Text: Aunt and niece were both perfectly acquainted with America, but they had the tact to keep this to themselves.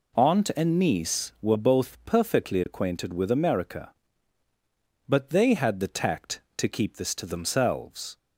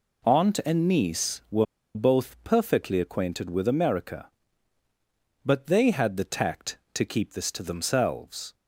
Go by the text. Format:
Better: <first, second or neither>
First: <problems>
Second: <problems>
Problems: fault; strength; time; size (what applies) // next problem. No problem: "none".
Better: first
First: none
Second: pauses between "were" and "both"; slight; at 1.6 s; 0.30 s long